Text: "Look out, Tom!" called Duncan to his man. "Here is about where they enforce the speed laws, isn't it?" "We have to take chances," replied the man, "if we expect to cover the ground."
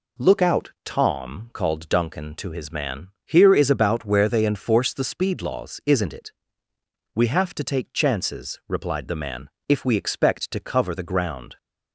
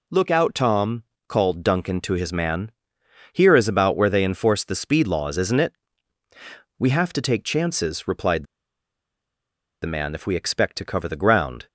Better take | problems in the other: first | pauses between "replied" and "the"; strong; at 8.4 s; 1.3 s long

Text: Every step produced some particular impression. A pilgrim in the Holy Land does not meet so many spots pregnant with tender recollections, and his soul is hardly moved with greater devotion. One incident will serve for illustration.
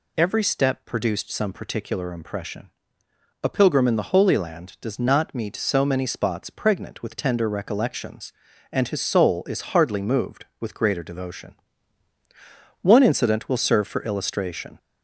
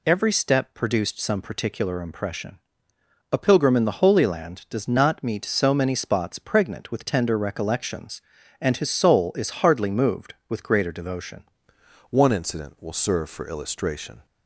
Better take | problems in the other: first | changes voice at "One"; from 12.1 s on; 2.1 s long

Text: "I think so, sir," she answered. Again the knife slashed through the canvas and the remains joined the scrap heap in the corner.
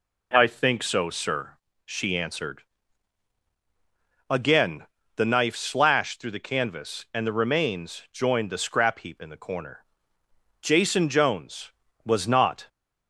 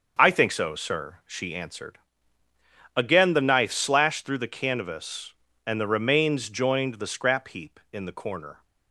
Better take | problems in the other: second | pauses between "Again" and "the"; slight; at 4.8 s; 0.30 s long // goes on to say "Jason Jones was not"; strong; from 10.6 s on; 2.0 s long

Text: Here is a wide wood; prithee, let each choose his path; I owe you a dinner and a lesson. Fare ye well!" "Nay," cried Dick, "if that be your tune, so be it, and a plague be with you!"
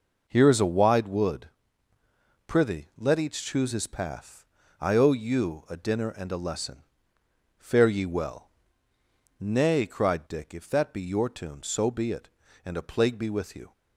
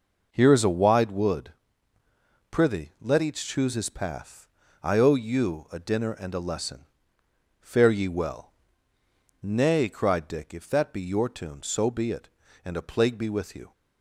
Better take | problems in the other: neither | none

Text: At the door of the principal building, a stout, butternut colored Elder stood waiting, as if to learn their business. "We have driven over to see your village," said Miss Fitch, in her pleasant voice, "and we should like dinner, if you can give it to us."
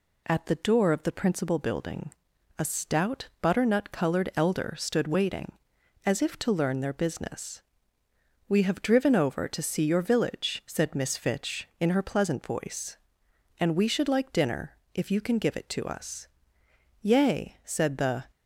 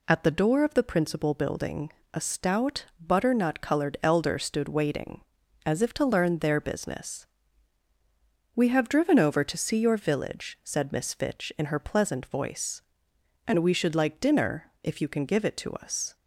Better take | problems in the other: second | goes on to say "Yea said the"; noticeable; from 17.0 s on; 1.2 s long

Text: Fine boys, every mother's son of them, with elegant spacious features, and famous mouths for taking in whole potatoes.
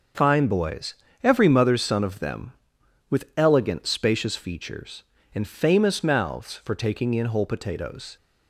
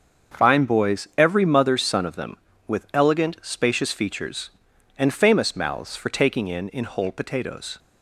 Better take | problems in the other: first | starts louder than the rest; until 1.4 s; 7 dB; also in the first // says "in" twice; at 6.7 s

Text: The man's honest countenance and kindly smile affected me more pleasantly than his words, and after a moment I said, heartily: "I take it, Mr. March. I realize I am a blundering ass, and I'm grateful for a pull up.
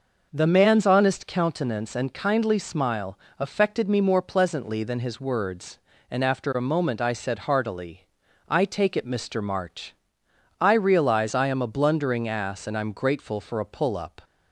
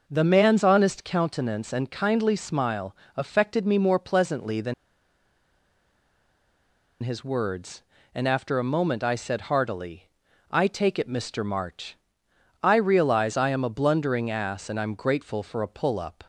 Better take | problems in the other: first | pauses between "smile" and "affected"; slight; at 2.9 s; 0.22 s long; slight in the first // pauses between "than" and "his"; strong; at 4.7 s; 2.2 s long

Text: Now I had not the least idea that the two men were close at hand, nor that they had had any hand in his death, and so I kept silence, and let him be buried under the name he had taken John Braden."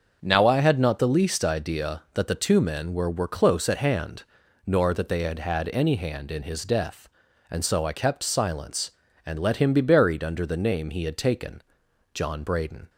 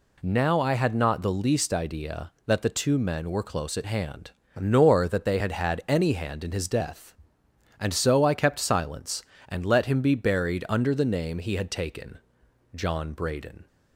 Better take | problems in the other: second | starts louder than the rest; until 1.2 s; 6.5 dB // says "were" twice; at 3.0 s // pauses between "taken" and "John"; noticeable; at 11.6 s; 0.52 s long; noticeable in the second

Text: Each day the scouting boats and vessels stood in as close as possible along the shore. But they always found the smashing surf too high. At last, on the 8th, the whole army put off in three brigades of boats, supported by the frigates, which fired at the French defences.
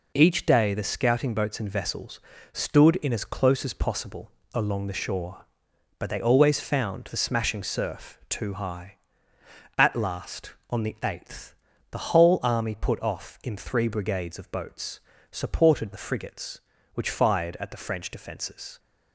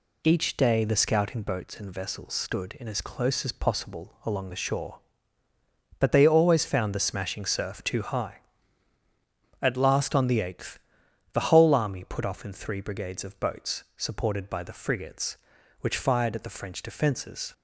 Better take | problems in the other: second | pauses between "vessels" and "stood"; slight; at 2.1 s; 0.32 s long // pauses between "possible" and "along"; slight; at 4.3 s; 0.22 s long // skips "by"; at 15.9 s

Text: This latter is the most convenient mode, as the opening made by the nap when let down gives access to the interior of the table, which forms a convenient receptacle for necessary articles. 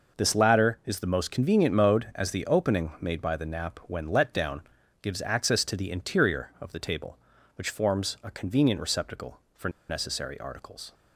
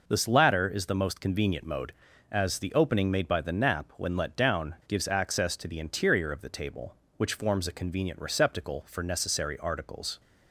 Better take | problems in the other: second | pauses between "down" and "gives"; at 4.6 s; 0.40 s long // pauses between "for" and "necessary"; slight; at 9.6 s; 0.19 s long

